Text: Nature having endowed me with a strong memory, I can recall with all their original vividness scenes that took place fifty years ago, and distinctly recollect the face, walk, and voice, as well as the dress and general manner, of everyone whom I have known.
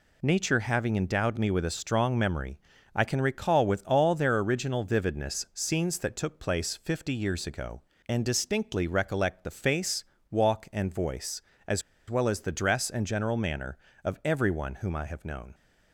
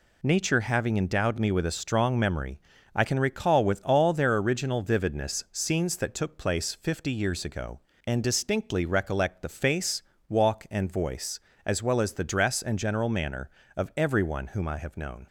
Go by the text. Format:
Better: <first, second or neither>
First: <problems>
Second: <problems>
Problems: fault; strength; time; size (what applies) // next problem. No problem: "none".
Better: second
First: pauses between "as" and "well"; slight; at 11.8 s; 0.28 s long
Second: none